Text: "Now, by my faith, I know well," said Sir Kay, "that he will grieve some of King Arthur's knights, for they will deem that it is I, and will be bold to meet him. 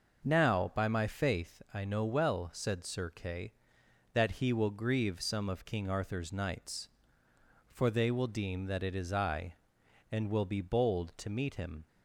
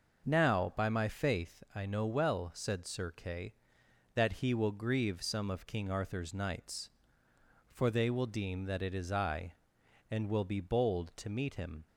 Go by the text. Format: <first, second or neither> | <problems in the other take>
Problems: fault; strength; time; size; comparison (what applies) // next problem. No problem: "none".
neither | none